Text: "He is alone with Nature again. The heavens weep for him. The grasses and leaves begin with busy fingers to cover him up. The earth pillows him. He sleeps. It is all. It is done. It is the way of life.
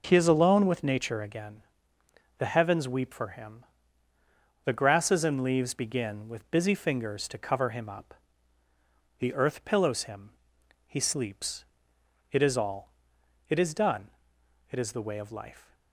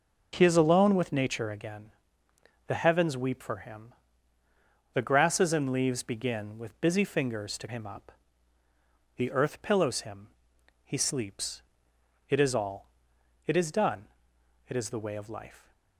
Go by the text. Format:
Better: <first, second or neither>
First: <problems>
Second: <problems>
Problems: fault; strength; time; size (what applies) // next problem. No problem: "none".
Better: first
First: none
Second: skips "cover"; at 7.6 s